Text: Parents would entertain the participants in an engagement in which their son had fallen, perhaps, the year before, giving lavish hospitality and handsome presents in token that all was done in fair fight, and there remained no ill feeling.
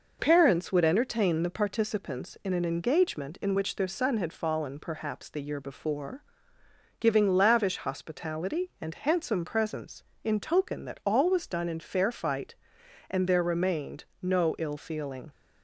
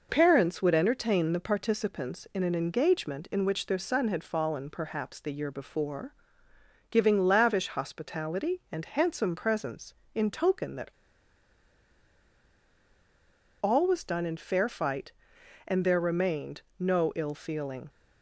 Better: first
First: pauses between "remained" and "no"; slight; at 14.0 s; 0.18 s long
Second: pauses between "that" and "all"; strong; at 10.9 s; 2.7 s long // pauses between "remained" and "no"; slight; at 16.6 s; 0.18 s long

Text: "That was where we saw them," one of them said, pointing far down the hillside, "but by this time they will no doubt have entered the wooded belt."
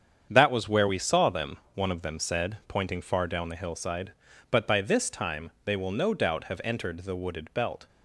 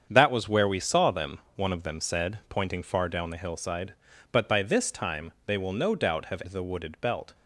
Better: first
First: starts louder than the rest; strong; until 1.3 s; 8 dB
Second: starts louder than the rest; strong; until 1.1 s; 7.5 dB // skips "entered"; at 6.4 s

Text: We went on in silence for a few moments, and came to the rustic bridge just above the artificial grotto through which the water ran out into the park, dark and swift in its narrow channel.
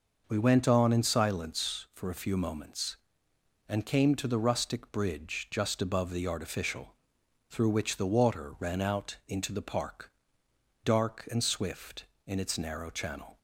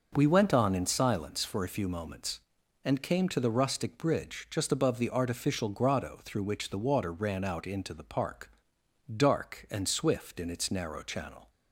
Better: second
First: skips "grotto"; at 7.2 s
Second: none

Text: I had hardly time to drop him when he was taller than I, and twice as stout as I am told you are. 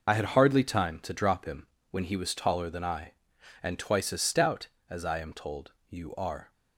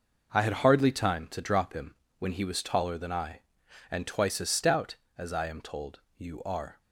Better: second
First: loses the start of "I"; at 0.0 s; 40 ms // pauses between "him" and "when"; slight; at 1.6 s; 0.24 s long // pauses between "told" and "you"; slight; at 5.7 s; 0.18 s long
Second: pauses between "him" and "when"; slight; at 1.9 s; 0.24 s long // pauses between "told" and "you"; slight; at 5.9 s; 0.18 s long

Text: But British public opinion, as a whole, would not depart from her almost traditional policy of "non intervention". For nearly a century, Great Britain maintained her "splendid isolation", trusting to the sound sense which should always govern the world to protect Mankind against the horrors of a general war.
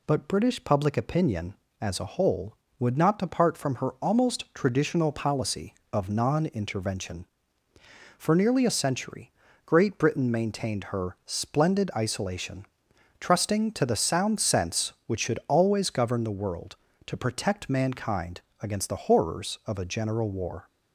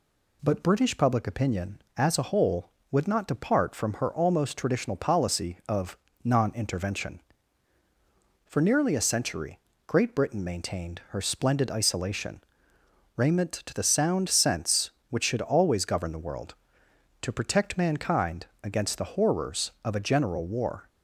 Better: first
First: pauses between "Mankind" and "against"; slight; at 18.4 s; 0.18 s long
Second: pauses between "of" and "non"; slight; at 5.9 s; 0.26 s long // says "raiment" for "trusting"; at 13.1 s // pauses between "Mankind" and "against"; slight; at 18.4 s; 0.18 s long

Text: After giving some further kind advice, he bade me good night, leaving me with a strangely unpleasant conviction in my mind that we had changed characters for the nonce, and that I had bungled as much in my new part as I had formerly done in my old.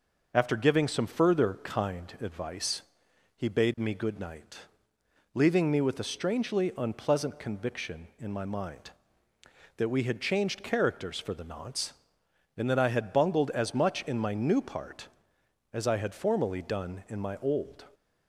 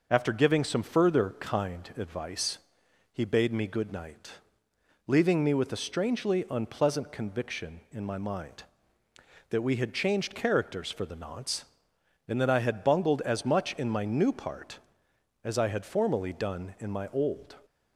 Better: neither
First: none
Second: none

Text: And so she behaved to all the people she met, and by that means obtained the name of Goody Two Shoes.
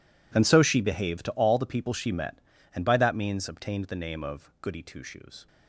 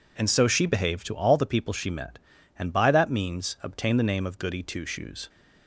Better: second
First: gets quieter; strong; throughout; 19 dB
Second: none

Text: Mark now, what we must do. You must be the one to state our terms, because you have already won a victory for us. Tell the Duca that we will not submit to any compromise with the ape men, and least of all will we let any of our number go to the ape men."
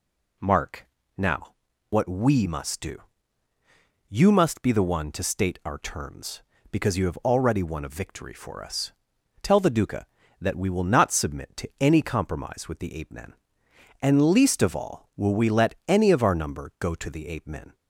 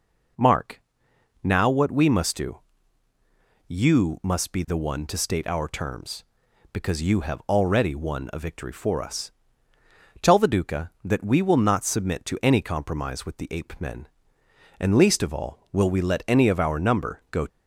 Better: first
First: pauses between "Mark" and "now"; slight; at 0.8 s; 0.30 s long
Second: pauses between "Mark" and "now"; noticeable; at 0.8 s; 0.62 s long // stops before "to the ape men"; at 17.4 s

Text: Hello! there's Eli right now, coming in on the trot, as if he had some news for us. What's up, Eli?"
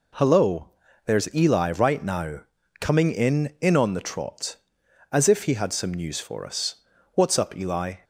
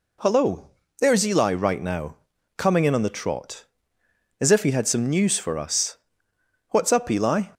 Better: second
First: says "in" twice; at 3.5 s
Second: none

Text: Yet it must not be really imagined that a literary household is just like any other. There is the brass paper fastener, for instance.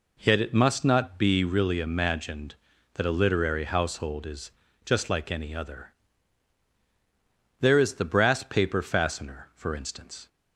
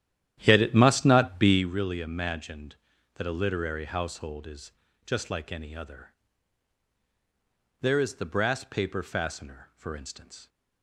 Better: first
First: pauses between "is" and "just"; slight; at 4.4 s; 0.34 s long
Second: starts louder than the rest; strong; until 1.6 s; 11.5 dB // pauses between "is" and "just"; slight; at 4.7 s; 0.34 s long

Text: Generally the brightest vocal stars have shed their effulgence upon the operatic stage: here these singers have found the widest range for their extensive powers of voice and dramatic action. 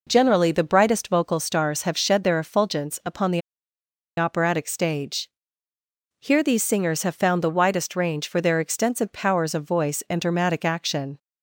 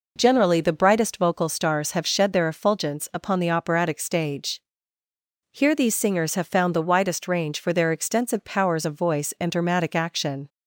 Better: second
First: pauses between "the" and "operatic"; noticeable; at 3.4 s; 0.77 s long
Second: none

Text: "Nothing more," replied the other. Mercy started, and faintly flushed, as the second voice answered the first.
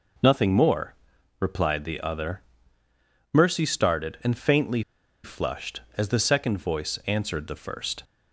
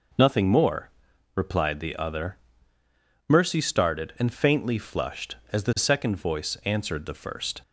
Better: second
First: pauses between "faintly" and "flushed"; at 4.8 s; 0.42 s long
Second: none

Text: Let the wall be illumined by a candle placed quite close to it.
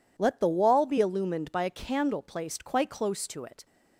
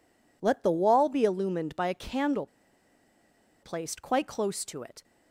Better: first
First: none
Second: pauses between "candle" and "placed"; at 2.4 s; 1.1 s long

